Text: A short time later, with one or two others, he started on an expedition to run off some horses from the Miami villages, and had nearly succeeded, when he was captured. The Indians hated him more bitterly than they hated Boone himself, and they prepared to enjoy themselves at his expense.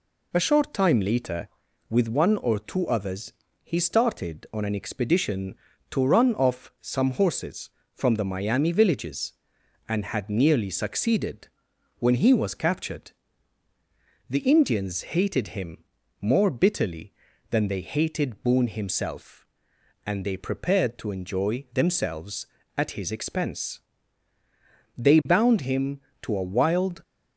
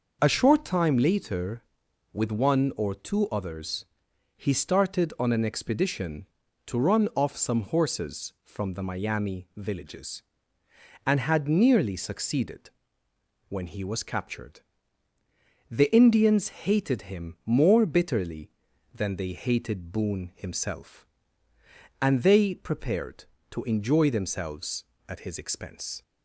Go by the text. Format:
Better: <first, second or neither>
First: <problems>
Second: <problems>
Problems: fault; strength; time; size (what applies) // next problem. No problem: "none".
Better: second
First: pauses between "him" and "more"; slight; at 15.8 s; 0.36 s long // goes on to say "They bound him to a wild"; strong; from 24.9 s on; 2.0 s long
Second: none